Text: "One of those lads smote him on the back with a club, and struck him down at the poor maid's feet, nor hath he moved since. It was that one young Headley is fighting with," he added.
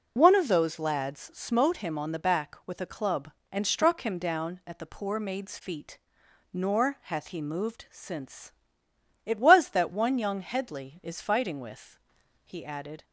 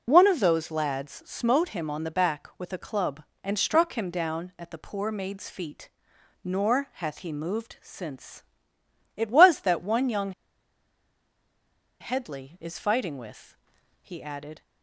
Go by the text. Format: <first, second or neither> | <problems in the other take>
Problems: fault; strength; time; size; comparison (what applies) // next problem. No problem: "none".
first | pauses between "young" and "Headley"; strong; at 10.3 s; 1.6 s long